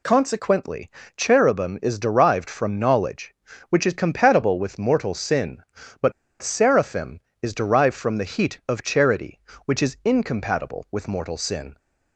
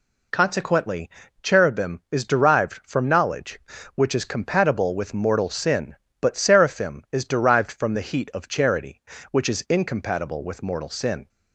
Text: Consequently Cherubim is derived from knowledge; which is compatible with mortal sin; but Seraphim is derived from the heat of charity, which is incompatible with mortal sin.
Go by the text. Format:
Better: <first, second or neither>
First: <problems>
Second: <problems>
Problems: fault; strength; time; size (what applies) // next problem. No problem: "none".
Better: second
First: pauses between "Consequently" and "Cherubim"; slight; at 0.8 s; 0.28 s long // pauses between "but" and "Seraphim"; slight; at 6.1 s; 0.30 s long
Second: pauses between "Consequently" and "Cherubim"; slight; at 1.1 s; 0.32 s long